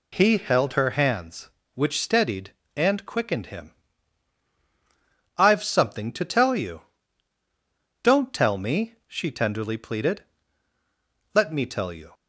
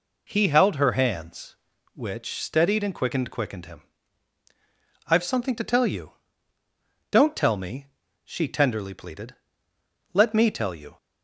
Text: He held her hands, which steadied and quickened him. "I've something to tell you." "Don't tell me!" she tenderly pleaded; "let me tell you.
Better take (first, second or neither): first